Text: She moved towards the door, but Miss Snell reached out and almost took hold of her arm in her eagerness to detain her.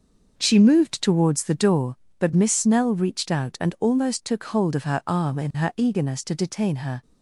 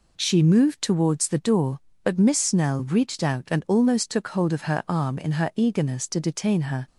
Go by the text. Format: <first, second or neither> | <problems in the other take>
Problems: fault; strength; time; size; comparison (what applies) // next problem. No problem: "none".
second | starts louder than the rest; noticeable; until 1.9 s; 6 dB